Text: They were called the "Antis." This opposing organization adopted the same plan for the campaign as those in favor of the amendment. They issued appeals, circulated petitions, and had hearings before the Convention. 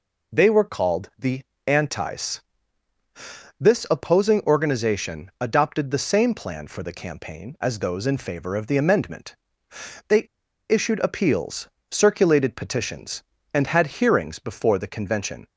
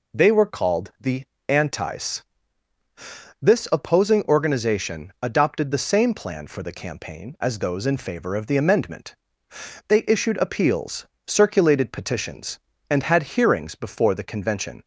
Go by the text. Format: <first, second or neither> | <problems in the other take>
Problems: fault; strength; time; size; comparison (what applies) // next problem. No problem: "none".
second | pauses between "the" and "Antis"; slight; at 1.4 s; 0.24 s long; slight in the second // pauses between "They" and "issued"; at 10.2 s; 0.44 s long